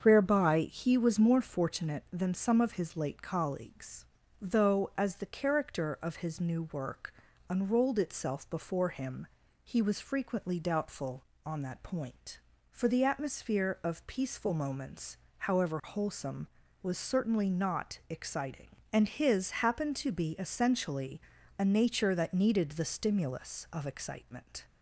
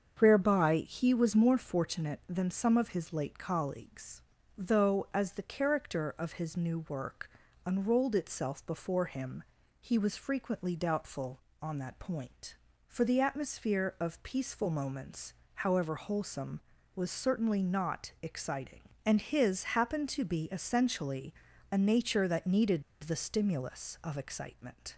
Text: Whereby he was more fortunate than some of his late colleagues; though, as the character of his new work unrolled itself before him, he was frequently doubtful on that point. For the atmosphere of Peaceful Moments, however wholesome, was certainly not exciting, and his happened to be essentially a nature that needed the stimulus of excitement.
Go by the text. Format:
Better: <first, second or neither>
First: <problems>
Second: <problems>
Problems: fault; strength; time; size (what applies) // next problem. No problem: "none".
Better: first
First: starts louder than the rest; until 1.0 s; 7 dB // pauses between "work" and "unrolled"; at 7.1 s; 0.38 s long // pauses between "his" and "happened"; slight; at 19.4 s; 0.16 s long // pauses between "essentially" and "a"; at 21.1 s; 0.38 s long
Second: starts louder than the rest; until 1.2 s; 7 dB // pauses between "work" and "unrolled"; at 7.2 s; 0.38 s long // pauses between "his" and "happened"; slight; at 19.6 s; 0.16 s long // pauses between "essentially" and "a"; at 21.3 s; 0.38 s long // pauses between "needed" and "the"; slight; at 22.8 s; 0.21 s long